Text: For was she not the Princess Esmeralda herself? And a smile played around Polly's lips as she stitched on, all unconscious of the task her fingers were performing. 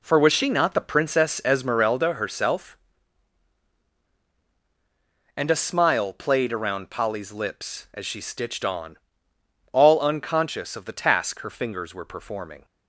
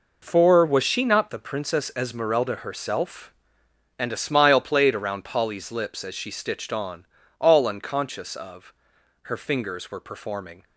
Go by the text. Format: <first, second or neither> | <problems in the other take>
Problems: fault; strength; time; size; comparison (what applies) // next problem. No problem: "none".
first | skips "the task"; at 8.9 s